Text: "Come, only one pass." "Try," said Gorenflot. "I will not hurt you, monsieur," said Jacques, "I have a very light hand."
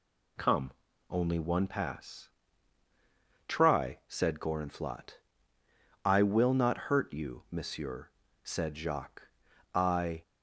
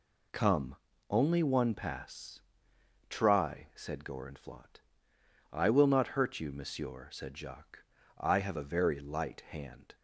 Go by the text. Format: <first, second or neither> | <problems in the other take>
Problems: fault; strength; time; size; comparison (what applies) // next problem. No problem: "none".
second | stops before "have a very light hand"; at 10.2 s